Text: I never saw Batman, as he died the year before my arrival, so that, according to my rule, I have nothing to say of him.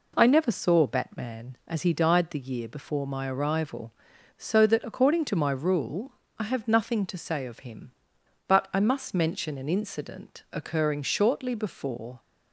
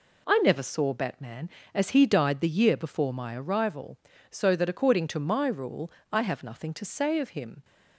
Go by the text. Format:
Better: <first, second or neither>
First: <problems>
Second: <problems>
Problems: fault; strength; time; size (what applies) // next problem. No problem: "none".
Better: second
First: goes on to say "But I must mention an incident occurring shortly before"; strong; from 8.4 s on; 3.7 s long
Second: none